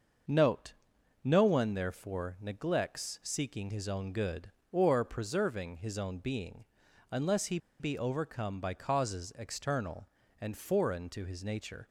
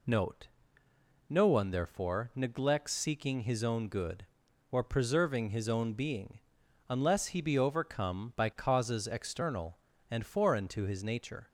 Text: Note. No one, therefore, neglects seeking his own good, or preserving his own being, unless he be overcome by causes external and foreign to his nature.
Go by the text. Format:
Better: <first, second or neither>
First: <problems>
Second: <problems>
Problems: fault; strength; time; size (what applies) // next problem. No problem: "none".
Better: second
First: starts louder than the rest; until 1.7 s; 6 dB // pauses between "he" and "be"; slight; at 7.5 s; 0.21 s long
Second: none